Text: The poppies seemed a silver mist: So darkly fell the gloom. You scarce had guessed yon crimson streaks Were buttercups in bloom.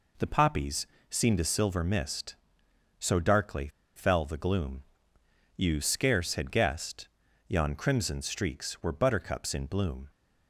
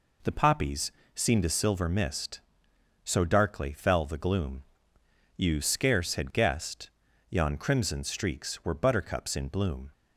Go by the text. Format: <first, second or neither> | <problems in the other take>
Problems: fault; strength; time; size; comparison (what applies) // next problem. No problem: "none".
second | pauses between "poppies" and "seemed"; slight; at 0.8 s; 0.24 s long; slight in the second // pauses between "darkly" and "fell"; slight; at 3.6 s; 0.27 s long // pauses between "guessed" and "yon"; at 7.0 s; 0.38 s long; also in the second